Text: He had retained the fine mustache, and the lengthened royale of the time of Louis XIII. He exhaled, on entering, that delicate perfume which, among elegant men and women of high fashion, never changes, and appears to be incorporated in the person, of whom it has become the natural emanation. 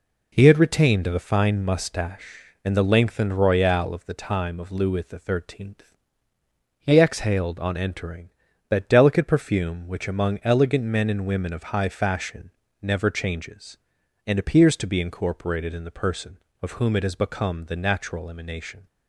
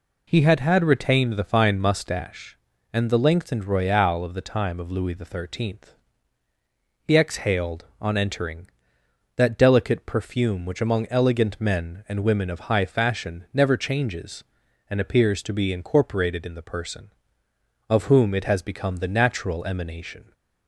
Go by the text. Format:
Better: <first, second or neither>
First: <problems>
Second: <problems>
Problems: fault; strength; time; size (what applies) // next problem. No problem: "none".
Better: first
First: none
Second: says "had" twice; at 0.5 s